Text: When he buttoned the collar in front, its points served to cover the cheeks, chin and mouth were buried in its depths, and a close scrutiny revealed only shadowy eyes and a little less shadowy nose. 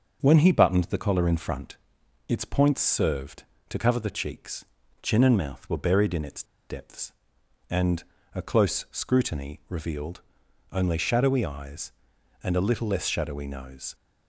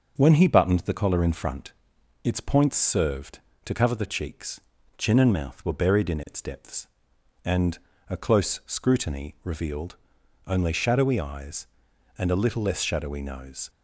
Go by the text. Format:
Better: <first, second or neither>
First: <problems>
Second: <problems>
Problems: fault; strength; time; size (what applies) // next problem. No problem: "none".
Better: second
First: pauses between "its" and "depths"; slight; at 6.4 s; 0.26 s long // pauses between "and" and "a"; slight; at 8.0 s; 0.32 s long // pauses between "revealed" and "only"; noticeable; at 10.2 s; 0.50 s long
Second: pauses between "and" and "a"; slight; at 7.7 s; 0.32 s long // pauses between "revealed" and "only"; noticeable; at 9.9 s; 0.50 s long